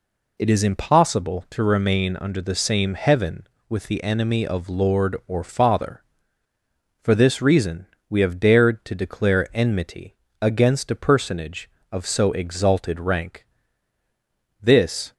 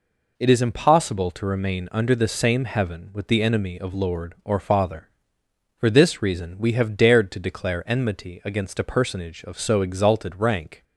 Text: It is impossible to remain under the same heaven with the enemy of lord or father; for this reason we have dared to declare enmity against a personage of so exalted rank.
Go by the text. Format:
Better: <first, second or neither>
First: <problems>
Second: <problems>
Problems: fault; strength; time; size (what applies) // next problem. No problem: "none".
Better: second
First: pauses between "reason" and "we"; slight; at 7.8 s; 0.20 s long // pauses between "enmity" and "against"; slight; at 10.1 s; 0.24 s long // goes on to say "This"; from 14.6 s on; 0.52 s long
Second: none